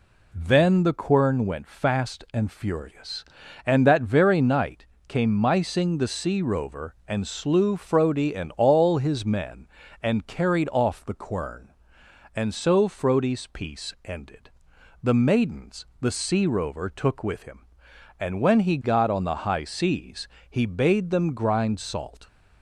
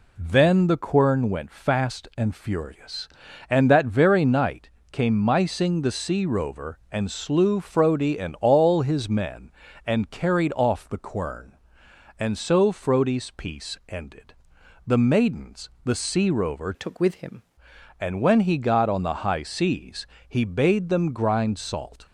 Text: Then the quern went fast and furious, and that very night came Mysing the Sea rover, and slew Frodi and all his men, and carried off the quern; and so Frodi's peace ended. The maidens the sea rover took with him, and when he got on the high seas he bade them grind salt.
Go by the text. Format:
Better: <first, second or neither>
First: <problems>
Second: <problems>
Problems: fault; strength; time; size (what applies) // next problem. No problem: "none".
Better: first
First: pauses between "night" and "came"; slight; at 4.8 s; 0.20 s long // pauses between "maidens" and "the"; slight; at 15.8 s; 0.16 s long // pauses between "seas" and "he"; slight; at 20.2 s; 0.24 s long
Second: pauses between "night" and "came"; slight; at 4.7 s; 0.20 s long // pauses between "maidens" and "the"; slight; at 15.6 s; 0.16 s long // changes voice from "took" to "him"; from 16.7 to 17.4 s; 0.7 s long // pauses between "seas" and "he"; slight; at 20.0 s; 0.24 s long